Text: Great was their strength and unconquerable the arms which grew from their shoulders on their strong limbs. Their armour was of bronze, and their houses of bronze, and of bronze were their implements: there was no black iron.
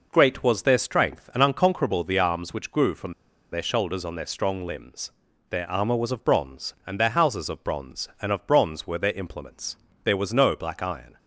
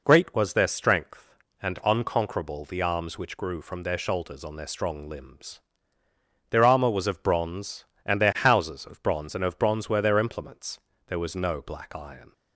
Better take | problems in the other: second | pauses between "from" and "their"; at 3.1 s; 0.39 s long

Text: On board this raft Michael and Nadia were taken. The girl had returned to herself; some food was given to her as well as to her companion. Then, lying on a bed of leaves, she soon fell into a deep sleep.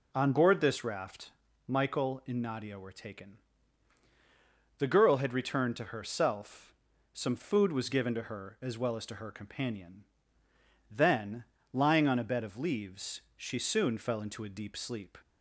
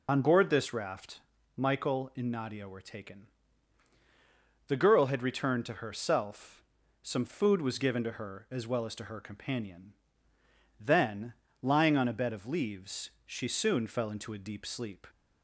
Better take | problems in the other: first | loses the start of "On"; at 0.0 s; 60 ms // pauses between "raft" and "Michael"; slight; at 1.1 s; 0.36 s long; slight in the first

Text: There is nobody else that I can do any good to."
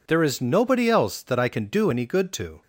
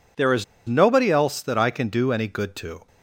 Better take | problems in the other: first | pauses between "is" and "nobody"; slight; at 0.4 s; 0.22 s long

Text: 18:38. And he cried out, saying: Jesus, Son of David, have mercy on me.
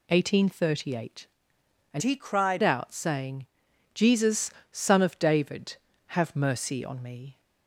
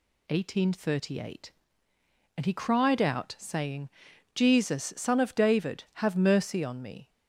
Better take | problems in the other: second | changes voice from "he" to "cried"; from 2.0 to 2.6 s; 0.6 s long

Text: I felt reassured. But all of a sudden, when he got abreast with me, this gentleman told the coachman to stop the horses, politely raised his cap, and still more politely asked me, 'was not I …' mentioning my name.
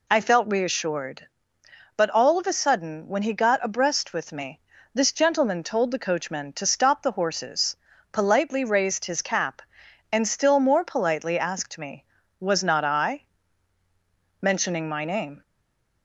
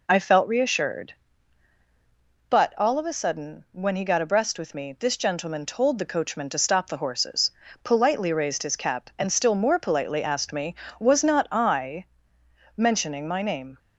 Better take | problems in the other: second | stays silent after the last word; slight; from 15.4 s on; 0.6 s long

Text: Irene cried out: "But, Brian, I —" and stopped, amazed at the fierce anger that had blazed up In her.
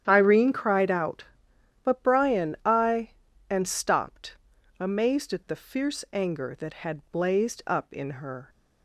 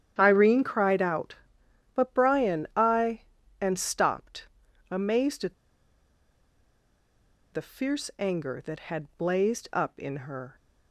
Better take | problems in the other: first | starts louder than the rest; strong; until 1.1 s; 9.5 dB; strong in the first // pauses between "at" and "the"; strong; at 5.5 s; 2.0 s long

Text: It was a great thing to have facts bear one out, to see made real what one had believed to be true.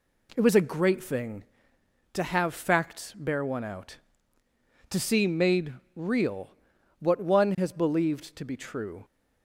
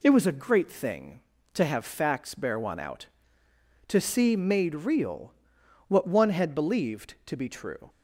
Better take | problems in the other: second | pauses between "made" and "real"; slight; at 5.7 s; 0.24 s long // pauses between "real" and "what"; noticeable; at 6.5 s; 0.50 s long; noticeable in the second // says "has" for "had"; at 7.5 s

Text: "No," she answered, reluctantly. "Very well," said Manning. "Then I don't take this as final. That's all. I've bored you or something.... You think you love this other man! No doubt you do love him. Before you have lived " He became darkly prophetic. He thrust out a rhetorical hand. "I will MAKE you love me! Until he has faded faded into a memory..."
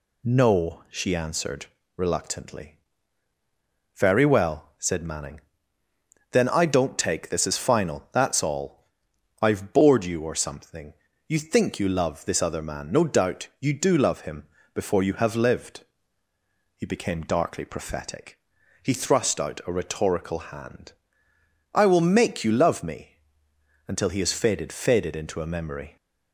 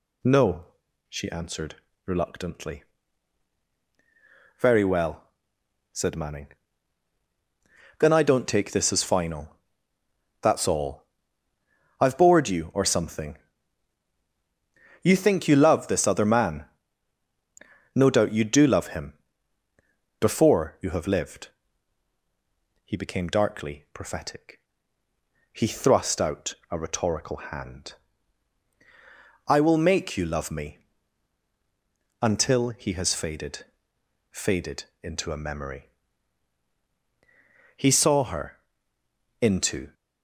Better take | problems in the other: first | pauses between "out" and "a"; slight; at 26.5 s; 0.16 s long // pauses between "faded" and "faded"; noticeable; at 33.6 s; 0.64 s long // pauses between "faded" and "into"; slight; at 34.8 s; 0.18 s long // goes on to say "He saw her into"; strong; from 37.7 s on; 2.1 s long

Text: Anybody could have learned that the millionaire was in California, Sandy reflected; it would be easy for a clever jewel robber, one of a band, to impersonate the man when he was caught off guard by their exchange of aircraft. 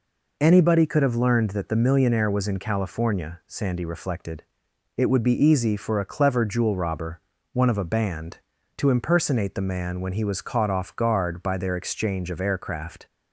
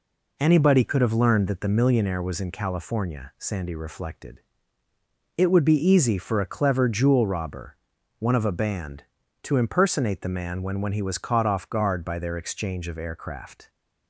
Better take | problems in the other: first | says "when" twice; at 10.8 s

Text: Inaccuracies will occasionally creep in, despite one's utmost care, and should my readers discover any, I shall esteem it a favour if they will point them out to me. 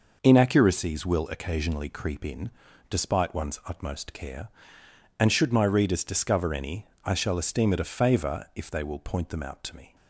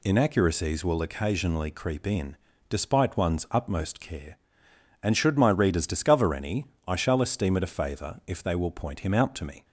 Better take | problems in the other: first | says "him" for "them"; at 9.0 s

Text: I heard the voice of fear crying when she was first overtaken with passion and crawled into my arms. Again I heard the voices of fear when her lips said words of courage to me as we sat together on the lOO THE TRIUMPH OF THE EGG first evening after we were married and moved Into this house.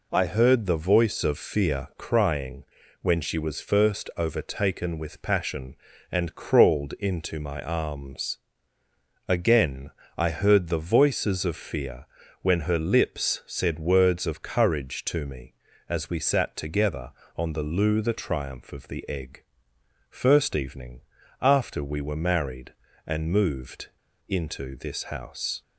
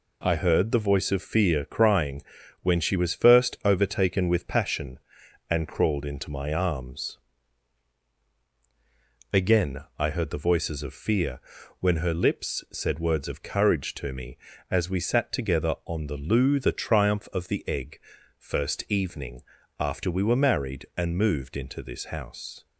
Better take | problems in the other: second | pauses between "crying" and "when"; at 2.6 s; 0.38 s long; also in the second // pauses between "Again" and "I"; slight; at 9.9 s; 0.26 s long; slight in the second // pauses between "fear" and "when"; slight; at 12.0 s; 0.36 s long; also in the second // pauses between "EGG" and "first"; noticeable; at 19.4 s; 0.66 s long; also in the second // pauses between "evening" and "after"; at 21.0 s; 0.40 s long; also in the second // pauses between "moved" and "Into"; at 23.8 s; 0.38 s long

